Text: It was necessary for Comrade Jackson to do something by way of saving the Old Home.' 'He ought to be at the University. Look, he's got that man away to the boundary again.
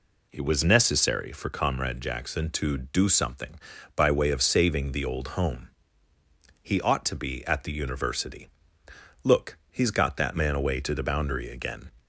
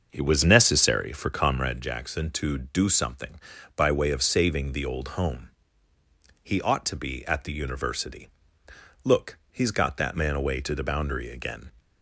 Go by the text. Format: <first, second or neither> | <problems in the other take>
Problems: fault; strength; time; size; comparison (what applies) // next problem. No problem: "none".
first | starts louder than the rest; until 1.9 s; 6.5 dB